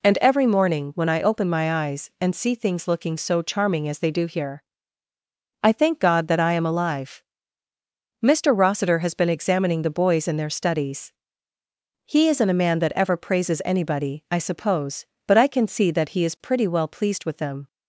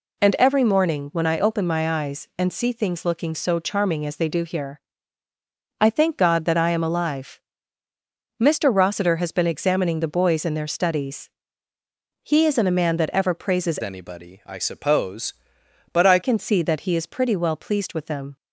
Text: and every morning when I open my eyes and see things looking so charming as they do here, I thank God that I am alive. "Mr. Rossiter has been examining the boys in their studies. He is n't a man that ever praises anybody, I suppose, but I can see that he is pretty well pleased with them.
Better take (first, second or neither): first